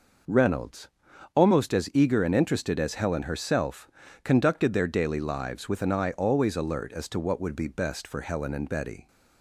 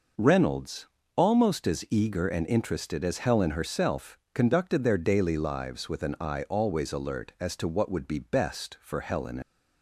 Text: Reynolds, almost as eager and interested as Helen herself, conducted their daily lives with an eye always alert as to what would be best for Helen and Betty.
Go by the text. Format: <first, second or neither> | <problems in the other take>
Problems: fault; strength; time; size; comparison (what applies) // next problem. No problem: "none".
first | stops before "and Betty"; at 9.4 s